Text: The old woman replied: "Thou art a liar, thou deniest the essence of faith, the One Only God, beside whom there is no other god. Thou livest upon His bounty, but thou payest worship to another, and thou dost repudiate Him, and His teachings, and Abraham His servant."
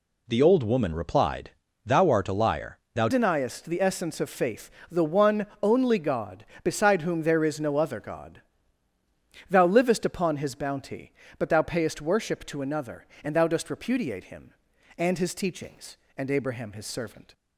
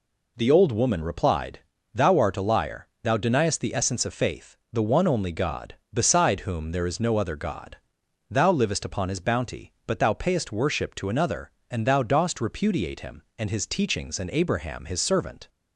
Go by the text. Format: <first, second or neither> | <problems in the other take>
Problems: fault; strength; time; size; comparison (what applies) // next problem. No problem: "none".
second | changes voice at "deniest"; from 3.0 s on; 14.3 s long // pauses between "One" and "Only"; slight; at 5.4 s; 0.16 s long